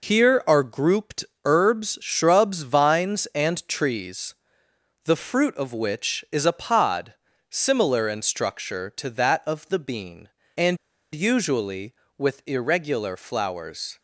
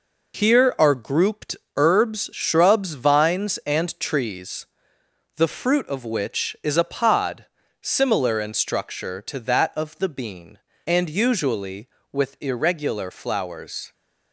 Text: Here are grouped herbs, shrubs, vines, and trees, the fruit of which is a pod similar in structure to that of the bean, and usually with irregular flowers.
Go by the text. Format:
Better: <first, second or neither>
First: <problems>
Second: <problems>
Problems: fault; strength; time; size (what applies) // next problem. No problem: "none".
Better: second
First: pauses between "grouped" and "herbs"; slight; at 1.2 s; 0.22 s long // pauses between "pod" and "similar"; slight; at 7.1 s; 0.34 s long // pauses between "and" and "usually"; slight; at 10.7 s; 0.36 s long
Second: pauses between "grouped" and "herbs"; slight; at 1.5 s; 0.22 s long // pauses between "pod" and "similar"; slight; at 7.4 s; 0.34 s long